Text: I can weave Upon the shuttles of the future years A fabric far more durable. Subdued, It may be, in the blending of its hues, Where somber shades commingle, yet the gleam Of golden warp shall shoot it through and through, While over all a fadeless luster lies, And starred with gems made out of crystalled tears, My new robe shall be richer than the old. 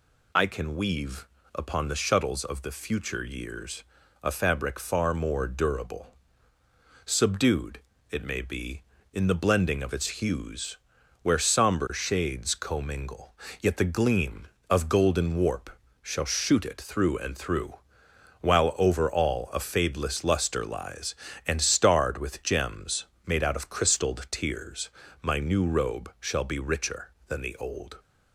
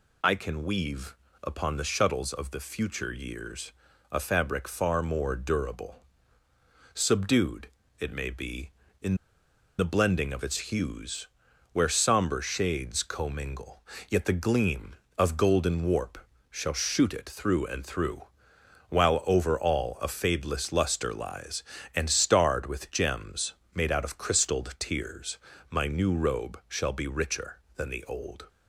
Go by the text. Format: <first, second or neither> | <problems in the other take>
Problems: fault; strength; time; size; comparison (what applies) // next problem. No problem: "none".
first | pauses between "weave" and "Upon"; slight; at 1.1 s; 0.26 s long; slight in the first // pauses between "years" and "A"; at 3.7 s; 0.40 s long; also in the first // pauses between "in" and "the"; noticeable; at 9.1 s; 0.63 s long // pauses between "warp" and "shall"; slight; at 16.1 s; 0.32 s long; slight in the first // pauses between "gems" and "made"; slight; at 23.5 s; 0.20 s long; slight in the first